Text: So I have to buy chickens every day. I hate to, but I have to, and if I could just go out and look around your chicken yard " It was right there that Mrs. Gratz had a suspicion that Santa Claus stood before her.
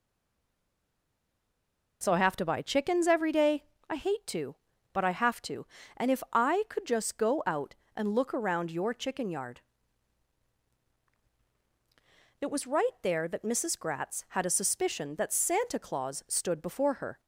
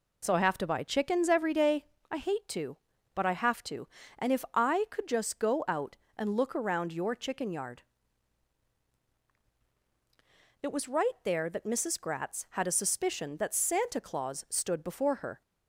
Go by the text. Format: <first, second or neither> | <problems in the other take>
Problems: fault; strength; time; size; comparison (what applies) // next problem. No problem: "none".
second | stays silent before the first word; noticeable; until 2.0 s; 2.0 s long